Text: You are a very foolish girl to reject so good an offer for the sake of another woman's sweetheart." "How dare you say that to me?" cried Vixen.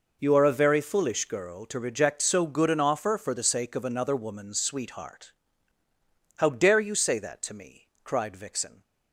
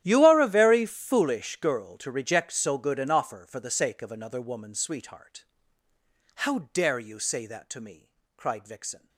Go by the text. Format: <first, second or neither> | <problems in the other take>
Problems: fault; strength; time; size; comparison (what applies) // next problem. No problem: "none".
first | gets quieter; strong; throughout; 21 dB